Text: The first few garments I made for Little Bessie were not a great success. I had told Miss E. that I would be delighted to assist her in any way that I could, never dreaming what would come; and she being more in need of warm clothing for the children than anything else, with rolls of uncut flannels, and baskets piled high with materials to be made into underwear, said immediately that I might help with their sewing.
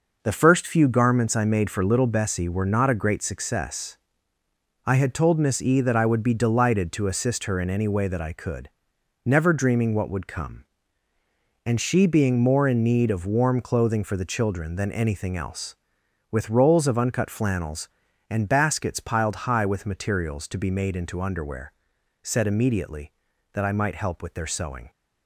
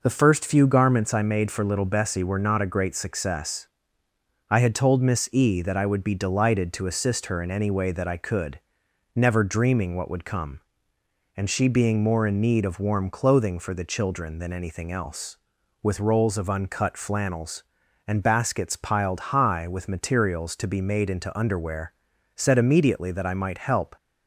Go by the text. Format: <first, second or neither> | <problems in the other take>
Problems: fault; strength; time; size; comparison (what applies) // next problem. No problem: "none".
first | stops before "with their sewing"; at 23.9 s